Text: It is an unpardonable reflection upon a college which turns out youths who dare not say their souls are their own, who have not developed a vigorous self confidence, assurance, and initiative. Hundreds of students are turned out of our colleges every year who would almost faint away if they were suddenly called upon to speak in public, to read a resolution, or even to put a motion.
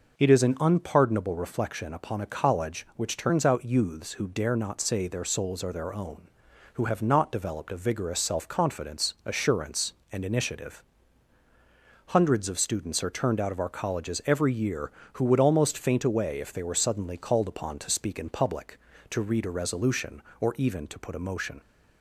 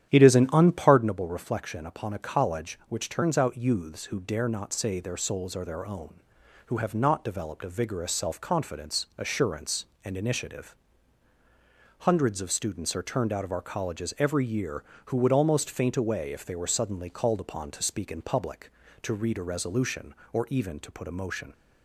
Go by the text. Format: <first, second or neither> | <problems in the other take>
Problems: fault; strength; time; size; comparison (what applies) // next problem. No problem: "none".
first | starts louder than the rest; strong; until 1.1 s; 10 dB